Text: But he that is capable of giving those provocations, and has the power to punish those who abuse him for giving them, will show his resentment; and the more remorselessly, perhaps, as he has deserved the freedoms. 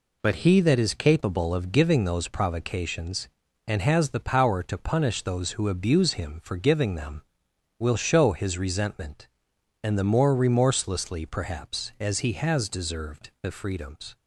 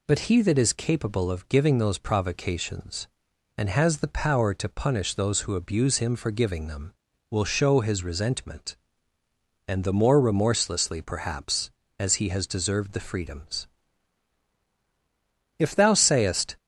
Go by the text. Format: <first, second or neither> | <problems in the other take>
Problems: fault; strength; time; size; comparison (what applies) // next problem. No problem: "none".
first | goes on to say "If thou sayest"; noticeable; from 15.5 s on; 1.0 s long